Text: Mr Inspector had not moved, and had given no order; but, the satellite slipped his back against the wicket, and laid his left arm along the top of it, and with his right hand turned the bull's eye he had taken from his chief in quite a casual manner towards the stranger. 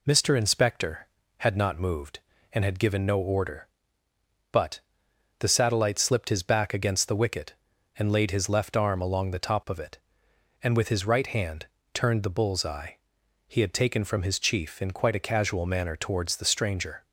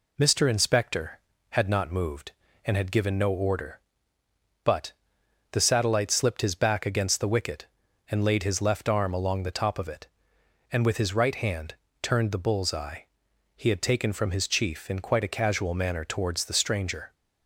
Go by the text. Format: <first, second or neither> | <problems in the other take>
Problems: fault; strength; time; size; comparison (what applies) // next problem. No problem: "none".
neither | pauses between "hand" and "turned"; slight; the same in both // pauses between "eye" and "he"; noticeable; the same in both